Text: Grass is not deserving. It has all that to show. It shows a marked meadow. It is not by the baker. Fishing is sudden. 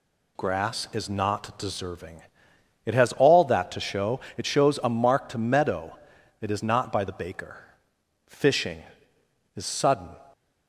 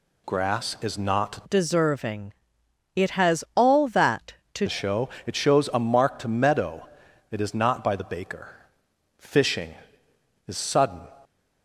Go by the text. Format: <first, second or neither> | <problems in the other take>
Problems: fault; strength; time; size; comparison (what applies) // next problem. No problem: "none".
first | changes voice from "deserving" to "to"; from 1.4 to 4.6 s; 3.2 s long